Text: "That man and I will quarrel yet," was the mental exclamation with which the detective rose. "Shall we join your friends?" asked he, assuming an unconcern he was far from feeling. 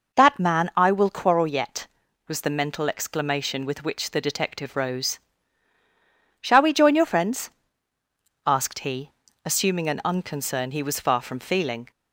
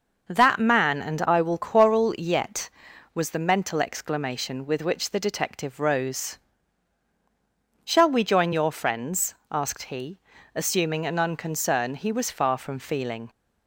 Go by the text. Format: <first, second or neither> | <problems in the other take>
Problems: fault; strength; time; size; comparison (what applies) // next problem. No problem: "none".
second | skips "and"; at 0.7 s